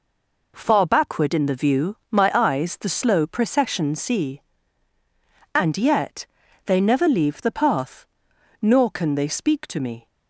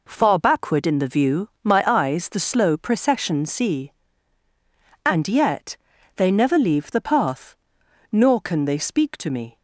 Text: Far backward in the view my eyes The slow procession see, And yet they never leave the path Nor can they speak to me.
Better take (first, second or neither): second